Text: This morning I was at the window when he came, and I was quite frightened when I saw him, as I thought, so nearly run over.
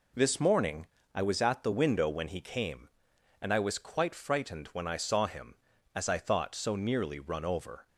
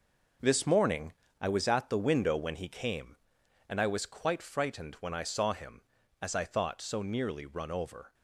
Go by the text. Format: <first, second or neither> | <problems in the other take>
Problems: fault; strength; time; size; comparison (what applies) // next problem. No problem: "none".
first | gets quieter; strong; throughout; 9 dB // pauses between "morning" and "I"; slight; at 1.1 s; 0.26 s long; slight in the first